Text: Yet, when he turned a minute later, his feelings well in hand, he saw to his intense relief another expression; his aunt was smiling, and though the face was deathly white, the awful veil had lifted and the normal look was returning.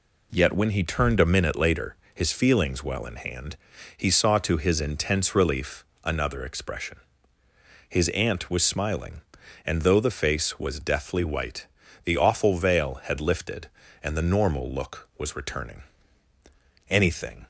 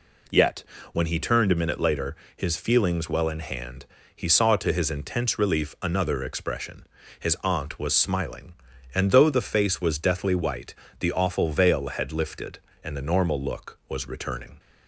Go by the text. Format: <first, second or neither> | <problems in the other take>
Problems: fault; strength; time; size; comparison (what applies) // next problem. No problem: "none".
second | pauses between "relief" and "another"; slight; at 5.8 s; 0.22 s long // goes on to say "Anything"; from 16.8 s on; 0.58 s long